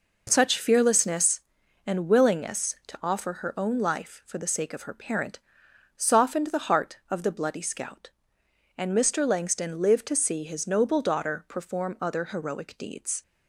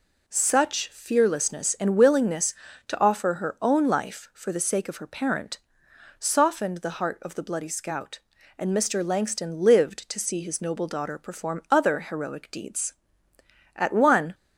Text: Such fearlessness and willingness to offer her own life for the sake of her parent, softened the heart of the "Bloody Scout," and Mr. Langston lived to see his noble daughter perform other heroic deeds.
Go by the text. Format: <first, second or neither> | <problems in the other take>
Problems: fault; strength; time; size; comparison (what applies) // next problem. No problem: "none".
first | goes on to say "At one"; from 13.7 s on; 0.58 s long